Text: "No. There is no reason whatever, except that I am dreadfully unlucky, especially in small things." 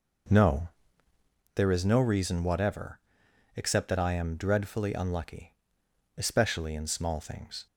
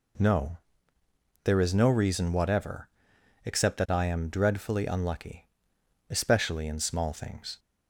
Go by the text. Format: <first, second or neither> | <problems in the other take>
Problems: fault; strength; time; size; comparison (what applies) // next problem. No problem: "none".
second | starts louder than the rest; noticeable; until 1.5 s; 5.5 dB